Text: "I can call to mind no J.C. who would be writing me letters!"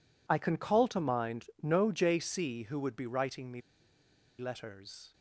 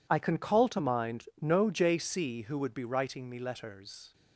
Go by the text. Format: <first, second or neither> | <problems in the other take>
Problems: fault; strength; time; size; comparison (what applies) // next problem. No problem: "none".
second | pauses between "mind" and "no"; slight; at 1.4 s; 0.16 s long; slight in the second // pauses between "me" and "letters"; noticeable; at 3.6 s; 0.78 s long